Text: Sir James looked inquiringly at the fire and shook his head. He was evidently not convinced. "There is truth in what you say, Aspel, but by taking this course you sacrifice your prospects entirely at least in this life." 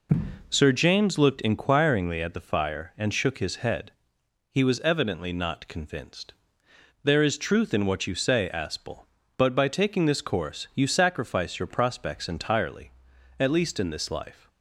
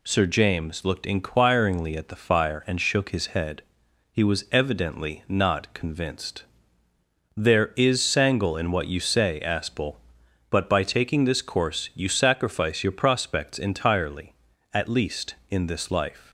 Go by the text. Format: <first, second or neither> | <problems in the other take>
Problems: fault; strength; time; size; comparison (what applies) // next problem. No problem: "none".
first | says "sangle" for "truth"; at 8.0 s